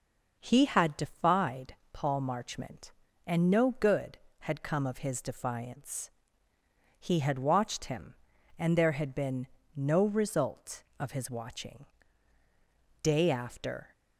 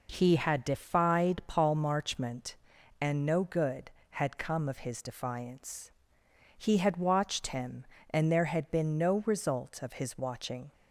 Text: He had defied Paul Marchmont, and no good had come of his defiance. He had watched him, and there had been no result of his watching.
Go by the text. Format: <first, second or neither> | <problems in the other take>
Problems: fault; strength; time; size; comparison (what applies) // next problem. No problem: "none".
second | pauses between "defied" and "Paul"; slight; at 1.7 s; 0.18 s long // pauses between "been" and "no"; slight; at 9.4 s; 0.28 s long // goes on to say "Day after"; noticeable; from 13.0 s on; 0.86 s long